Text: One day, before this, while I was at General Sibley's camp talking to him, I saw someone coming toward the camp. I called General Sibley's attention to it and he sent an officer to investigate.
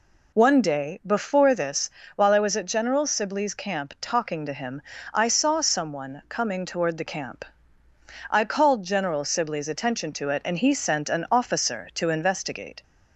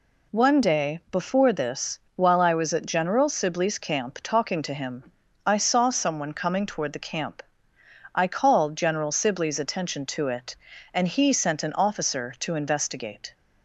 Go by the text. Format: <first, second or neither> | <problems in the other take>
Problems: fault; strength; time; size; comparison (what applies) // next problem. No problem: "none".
neither | none